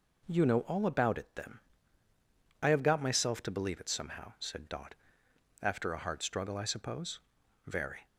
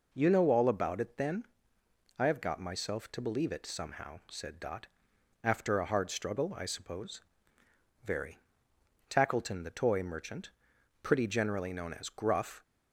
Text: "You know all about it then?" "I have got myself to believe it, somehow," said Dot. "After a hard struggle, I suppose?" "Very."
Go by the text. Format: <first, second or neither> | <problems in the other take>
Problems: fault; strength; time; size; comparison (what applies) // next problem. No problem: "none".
first | goes on to say "Tackleton the Toy merchant pretty generally known as Gruff"; strong; from 9.0 s on; 3.5 s long